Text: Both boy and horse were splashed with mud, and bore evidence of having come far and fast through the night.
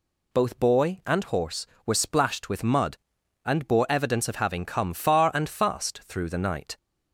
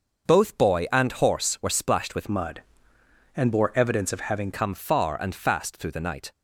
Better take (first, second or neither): first